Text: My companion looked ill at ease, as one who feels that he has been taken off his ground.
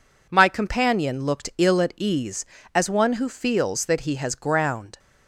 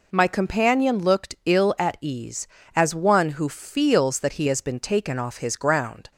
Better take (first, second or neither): second